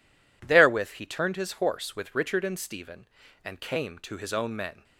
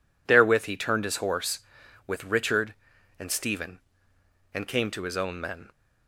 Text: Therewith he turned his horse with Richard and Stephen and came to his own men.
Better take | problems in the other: neither | none

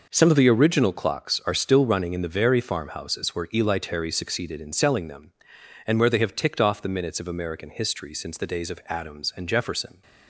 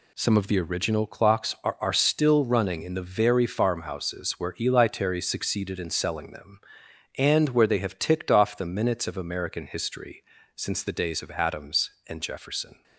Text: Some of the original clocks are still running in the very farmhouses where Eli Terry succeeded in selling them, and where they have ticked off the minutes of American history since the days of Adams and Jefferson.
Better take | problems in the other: first | says "are" twice; at 1.8 s // pauses between "history" and "since"; slight; at 10.2 s; 0.32 s long

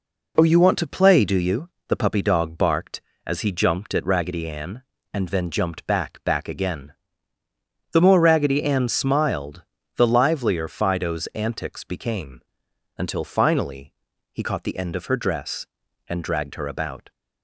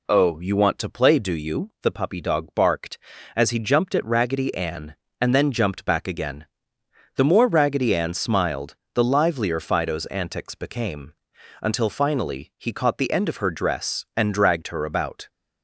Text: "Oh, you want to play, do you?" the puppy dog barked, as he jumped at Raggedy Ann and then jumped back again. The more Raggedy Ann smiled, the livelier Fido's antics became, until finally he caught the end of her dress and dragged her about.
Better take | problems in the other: second | says "back" twice; at 6.2 s // pauses between "finally" and "he"; at 13.9 s; 0.38 s long

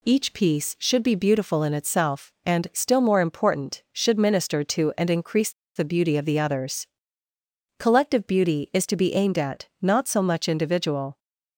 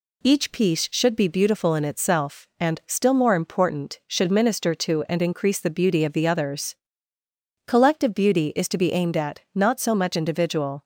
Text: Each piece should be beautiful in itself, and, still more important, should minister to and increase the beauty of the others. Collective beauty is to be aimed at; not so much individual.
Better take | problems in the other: second | pauses between "increase" and "the"; slight; at 5.5 s; 0.25 s long

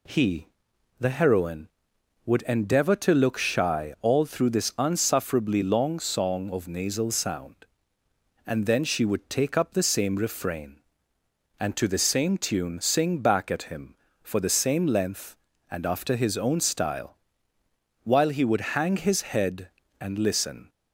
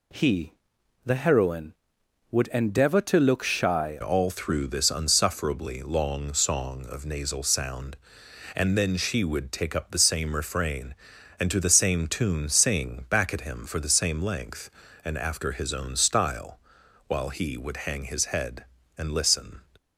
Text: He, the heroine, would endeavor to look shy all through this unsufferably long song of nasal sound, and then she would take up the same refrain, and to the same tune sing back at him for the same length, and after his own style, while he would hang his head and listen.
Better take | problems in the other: first | changes voice at "all"; from 4.0 s on; 15.6 s long

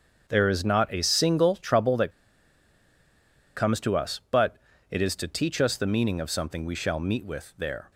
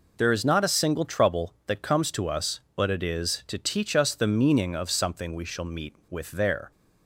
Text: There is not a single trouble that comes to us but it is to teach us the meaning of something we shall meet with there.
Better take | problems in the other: second | starts louder than the rest; until 1.2 s; 7 dB // pauses between "that" and "comes"; strong; at 2.1 s; 1.4 s long // pauses between "but" and "it"; slight; at 4.5 s; 0.34 s long

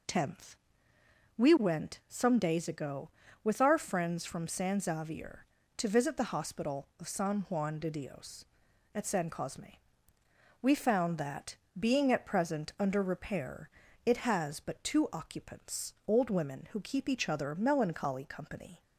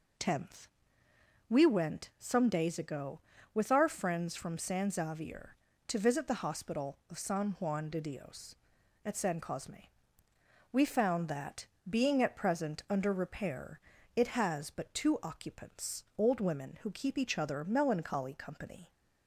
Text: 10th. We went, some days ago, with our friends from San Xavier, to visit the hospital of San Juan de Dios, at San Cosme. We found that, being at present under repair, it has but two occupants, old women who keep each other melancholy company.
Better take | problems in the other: neither | none

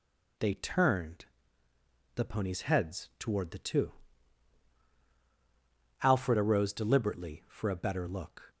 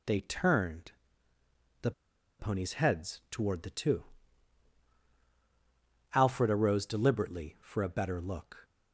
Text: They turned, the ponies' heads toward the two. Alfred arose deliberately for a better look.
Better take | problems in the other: first | pauses between "the" and "ponies"; noticeable; at 1.9 s; 0.48 s long

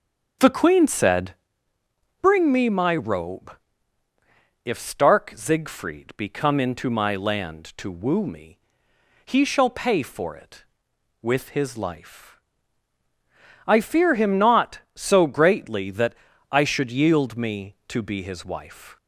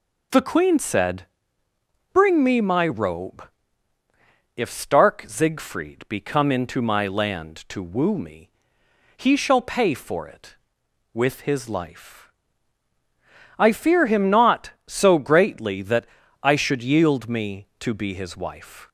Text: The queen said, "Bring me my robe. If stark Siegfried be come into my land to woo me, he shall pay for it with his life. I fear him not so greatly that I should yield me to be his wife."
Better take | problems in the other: second | starts louder than the rest; until 1.5 s; 6.5 dB // pauses between "that" and "I"; at 16.1 s; 0.38 s long; also in the second

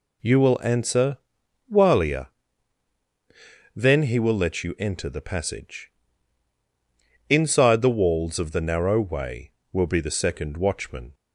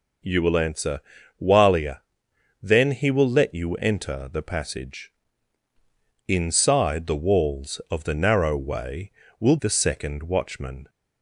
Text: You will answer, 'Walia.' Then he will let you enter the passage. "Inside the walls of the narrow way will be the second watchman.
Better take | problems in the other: first | skips "be"; at 9.5 s

